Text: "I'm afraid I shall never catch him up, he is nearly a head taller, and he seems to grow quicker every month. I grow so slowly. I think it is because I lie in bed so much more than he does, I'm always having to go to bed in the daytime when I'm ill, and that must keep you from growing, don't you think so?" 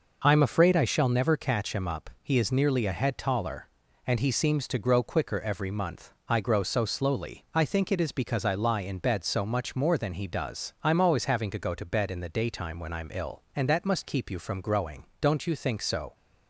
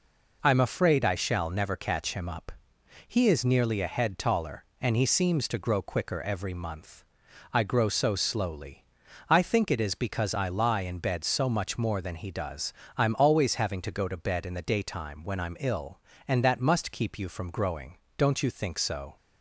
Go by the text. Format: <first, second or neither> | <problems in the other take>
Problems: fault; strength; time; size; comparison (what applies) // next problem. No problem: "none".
neither | none